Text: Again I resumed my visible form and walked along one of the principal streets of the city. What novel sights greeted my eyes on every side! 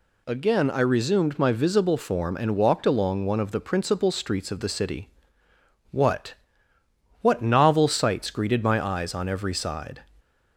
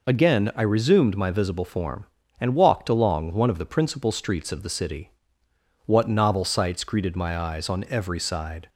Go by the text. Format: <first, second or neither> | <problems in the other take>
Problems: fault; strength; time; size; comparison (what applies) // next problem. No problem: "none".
second | says "What" twice; at 7.2 s